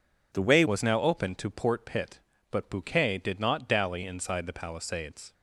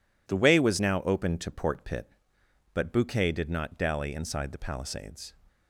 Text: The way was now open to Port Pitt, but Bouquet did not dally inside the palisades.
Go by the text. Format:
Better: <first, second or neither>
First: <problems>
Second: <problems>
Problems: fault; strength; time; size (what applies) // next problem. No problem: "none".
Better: second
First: changes voice at "was"; from 0.6 s on; 4.7 s long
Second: none